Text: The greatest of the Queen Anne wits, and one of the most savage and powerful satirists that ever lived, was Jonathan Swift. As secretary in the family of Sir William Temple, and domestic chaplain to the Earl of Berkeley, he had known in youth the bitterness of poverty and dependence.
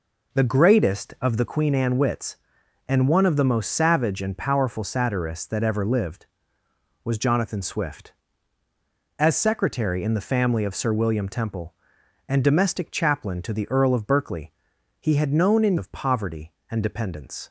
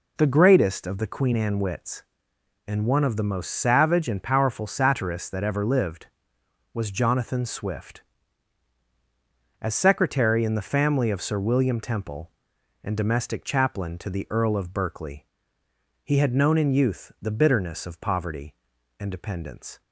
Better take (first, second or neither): second